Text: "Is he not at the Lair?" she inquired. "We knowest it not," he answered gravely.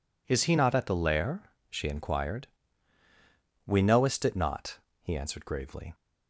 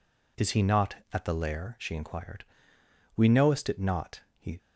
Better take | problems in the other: first | stops before "answered gravely"; at 4.5 s

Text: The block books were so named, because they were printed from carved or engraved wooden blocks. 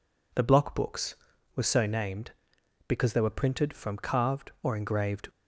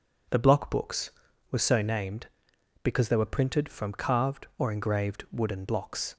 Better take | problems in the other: second | stops before "wooden blocks"; at 5.2 s

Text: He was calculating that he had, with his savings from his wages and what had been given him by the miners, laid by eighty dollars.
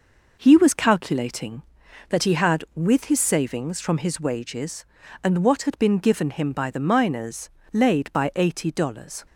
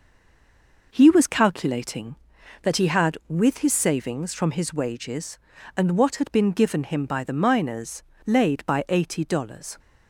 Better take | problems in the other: first | stays silent before the first word; slight; until 0.9 s; 0.9 s long

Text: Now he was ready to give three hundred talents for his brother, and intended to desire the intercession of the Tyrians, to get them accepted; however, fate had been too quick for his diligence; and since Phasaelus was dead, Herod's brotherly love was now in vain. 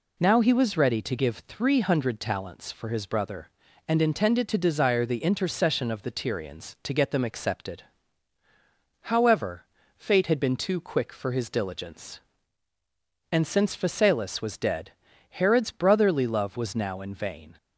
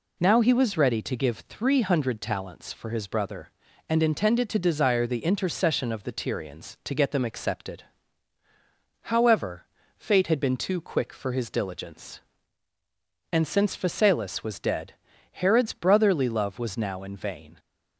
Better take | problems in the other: neither | none

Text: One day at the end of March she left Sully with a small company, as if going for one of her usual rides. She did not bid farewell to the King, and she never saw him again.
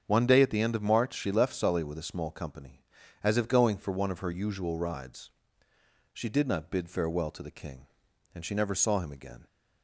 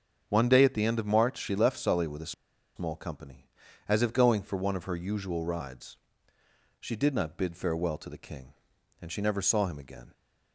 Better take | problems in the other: first | starts louder than the rest; strong; until 1.2 s; 7 dB; strong in the first // pauses between "a" and "small"; at 2.3 s; 0.44 s long

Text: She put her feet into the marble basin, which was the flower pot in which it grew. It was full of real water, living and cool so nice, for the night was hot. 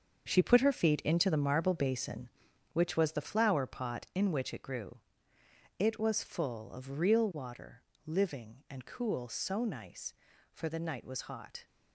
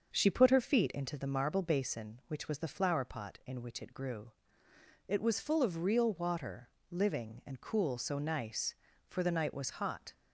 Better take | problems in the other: second | gets quieter; strong; throughout; 9.5 dB // starts louder than the rest; until 1.3 s; 7 dB; also in the second

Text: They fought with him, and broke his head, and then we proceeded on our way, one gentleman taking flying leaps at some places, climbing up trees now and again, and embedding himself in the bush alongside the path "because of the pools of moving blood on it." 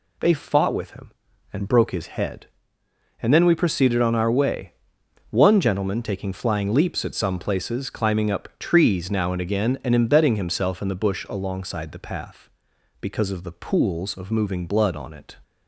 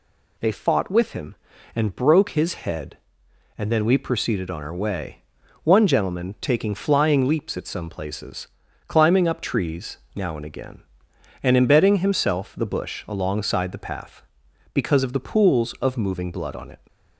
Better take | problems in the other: first | pauses between "trees" and "now"; slight; at 9.9 s; 0.18 s long // skips "in"; at 12.5 s

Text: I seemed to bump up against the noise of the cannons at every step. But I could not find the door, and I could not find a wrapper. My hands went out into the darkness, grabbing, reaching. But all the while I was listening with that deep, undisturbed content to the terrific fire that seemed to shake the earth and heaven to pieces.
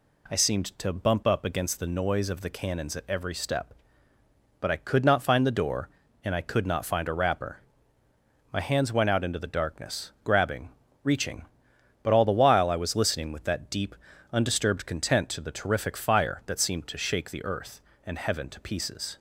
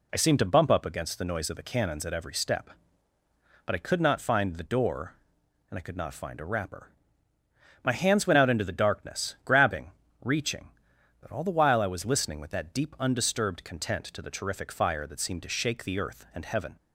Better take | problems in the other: first | stops before "to pieces"; at 16.7 s

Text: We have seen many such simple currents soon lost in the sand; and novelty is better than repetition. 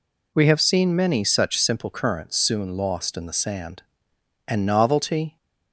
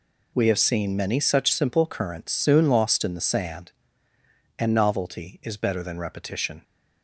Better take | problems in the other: second | stops before "is better than repetition"; at 5.3 s

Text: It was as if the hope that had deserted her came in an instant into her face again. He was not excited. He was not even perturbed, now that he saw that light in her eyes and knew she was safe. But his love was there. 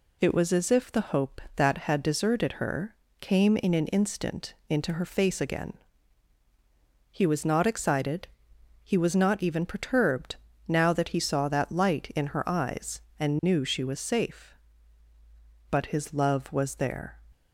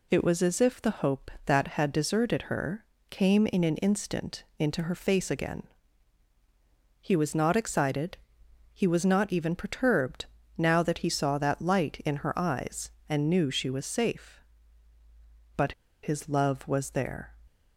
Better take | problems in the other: first | pauses between "her" and "came"; slight; at 2.8 s; 0.26 s long; slight in the first // pauses between "But" and "his"; slight; at 15.7 s; 0.30 s long

